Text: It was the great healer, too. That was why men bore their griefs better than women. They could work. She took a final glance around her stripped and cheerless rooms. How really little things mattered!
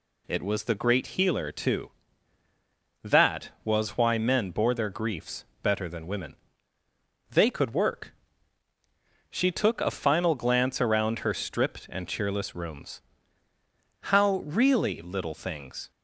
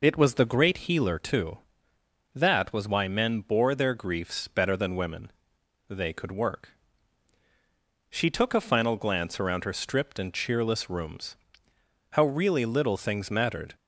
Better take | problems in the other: second | pauses between "griefs" and "better"; slight; at 5.4 s; 0.18 s long // stops before "mattered"; at 15.9 s

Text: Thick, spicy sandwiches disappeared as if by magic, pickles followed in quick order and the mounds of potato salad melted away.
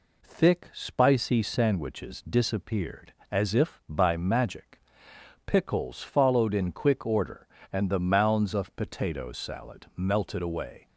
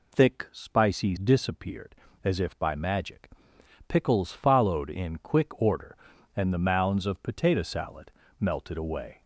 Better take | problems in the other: first | skips "sandwiches"; at 1.1 s // pauses between "salad" and "melted"; slight; at 8.0 s; 0.30 s long

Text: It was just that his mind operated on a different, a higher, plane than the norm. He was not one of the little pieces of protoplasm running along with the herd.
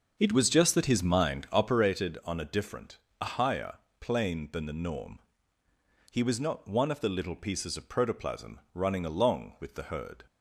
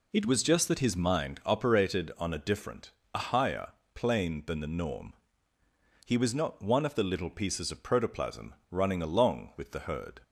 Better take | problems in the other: second | starts louder than the rest; until 1.8 s; 6.5 dB // pauses between "protoplasm" and "running"; slight; at 8.5 s; 0.16 s long; slight in the second

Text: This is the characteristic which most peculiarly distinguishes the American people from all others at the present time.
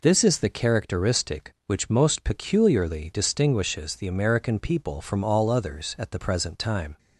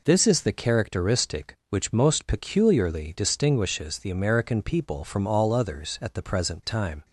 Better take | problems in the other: neither | none

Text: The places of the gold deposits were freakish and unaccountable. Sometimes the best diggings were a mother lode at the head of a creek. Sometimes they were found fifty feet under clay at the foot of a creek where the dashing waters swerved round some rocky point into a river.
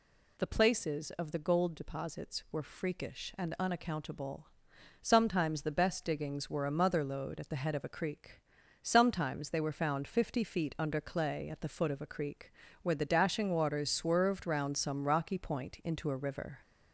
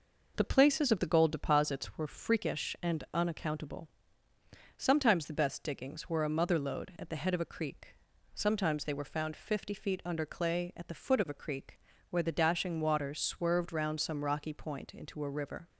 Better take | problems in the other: second | gets louder; slight; throughout; 3 dB // pauses between "creek" and "where"; slight; at 12.5 s; 0.30 s long; slight in the second

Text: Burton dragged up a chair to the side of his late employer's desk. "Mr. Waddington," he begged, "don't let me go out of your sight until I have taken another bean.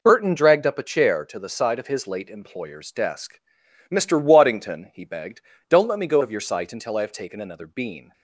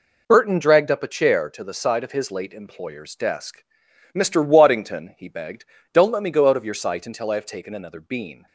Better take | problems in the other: second | skips "out"; at 6.2 s

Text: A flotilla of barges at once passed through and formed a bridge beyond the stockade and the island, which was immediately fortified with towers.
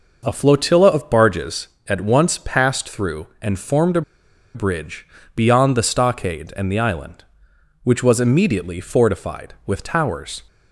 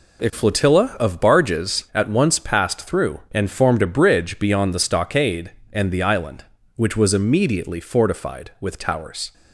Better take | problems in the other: second | pauses between "a" and "bridge"; noticeable; at 4.0 s; 0.52 s long // pauses between "bridge" and "beyond"; slight; at 5.0 s; 0.30 s long

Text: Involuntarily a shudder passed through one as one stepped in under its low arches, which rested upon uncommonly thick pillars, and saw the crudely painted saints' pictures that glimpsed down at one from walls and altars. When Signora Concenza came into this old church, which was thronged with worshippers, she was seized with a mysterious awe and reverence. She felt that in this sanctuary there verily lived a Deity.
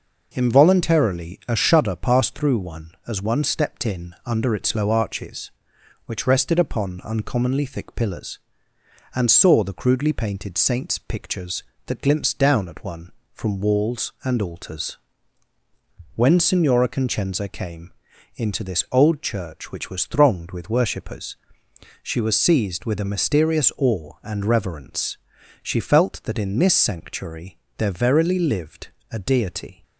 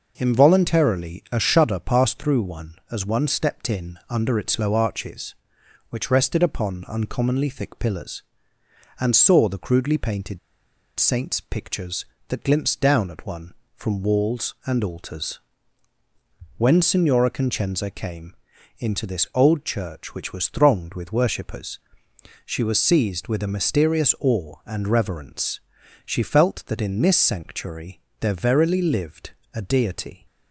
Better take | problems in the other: first | pauses between "painted" and "saints"; noticeable; at 10.3 s; 0.60 s long // pauses between "came" and "into"; at 18.3 s; 0.44 s long; also in the first // pauses between "sanctuary" and "there"; slight; at 28.0 s; 0.20 s long; slight in the first // pauses between "lived" and "a"; slight; at 29.3 s; 0.20 s long; slight in the first

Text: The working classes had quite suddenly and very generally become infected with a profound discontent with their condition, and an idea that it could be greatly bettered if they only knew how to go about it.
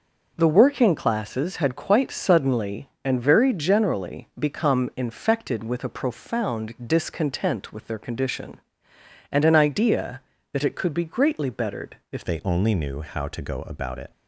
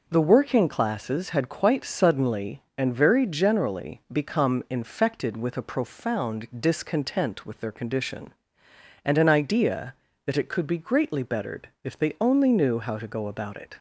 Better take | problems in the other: second | changes voice at "they"; from 12.2 s on; 1.9 s long

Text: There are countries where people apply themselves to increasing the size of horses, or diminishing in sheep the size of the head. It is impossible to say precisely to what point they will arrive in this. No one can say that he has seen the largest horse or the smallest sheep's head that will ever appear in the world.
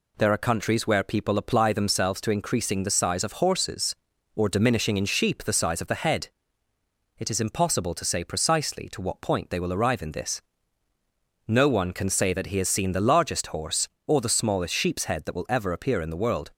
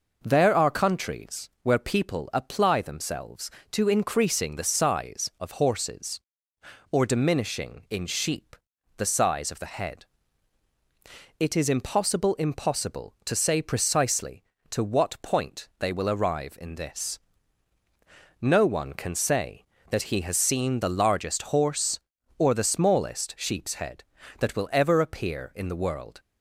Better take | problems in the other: first | pauses between "sheep" and "the"; at 8.5 s; 0.44 s long // says "impossible" twice; at 12.3 s

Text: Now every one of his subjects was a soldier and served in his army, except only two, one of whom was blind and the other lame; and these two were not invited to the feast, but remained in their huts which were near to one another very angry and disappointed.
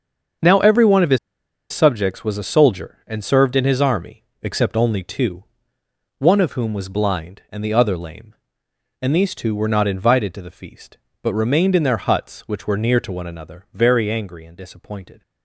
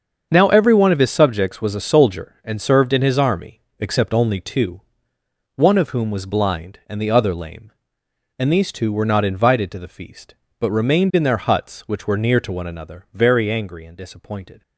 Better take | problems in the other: second | starts louder than the rest; until 1.9 s; 7 dB; also in the second // pauses between "his" and "subjects"; noticeable; at 1.1 s; 0.53 s long

